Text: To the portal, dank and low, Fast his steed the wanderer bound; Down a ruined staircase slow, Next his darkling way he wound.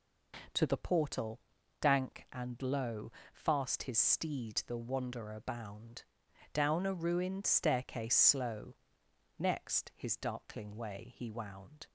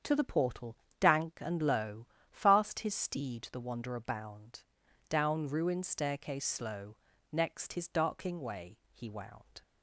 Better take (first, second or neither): first